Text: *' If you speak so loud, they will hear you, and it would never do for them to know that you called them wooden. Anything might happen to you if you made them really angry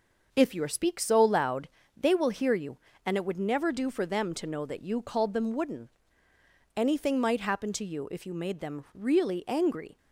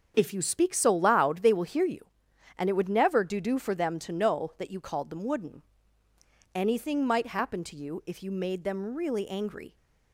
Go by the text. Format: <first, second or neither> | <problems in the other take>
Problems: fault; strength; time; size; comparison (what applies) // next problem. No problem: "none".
first | starts louder than the rest; strong; until 1.1 s; 7 dB // says "do" twice; at 3.4 s